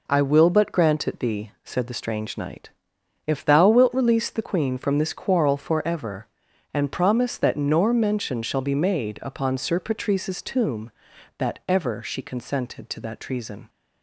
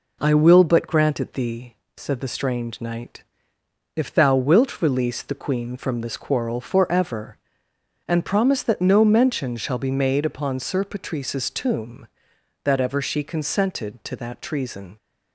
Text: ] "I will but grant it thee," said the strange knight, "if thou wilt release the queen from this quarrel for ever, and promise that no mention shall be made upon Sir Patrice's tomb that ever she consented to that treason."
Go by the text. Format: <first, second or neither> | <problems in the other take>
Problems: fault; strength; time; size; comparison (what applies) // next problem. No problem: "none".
second | says "nor" for "no"; at 7.5 s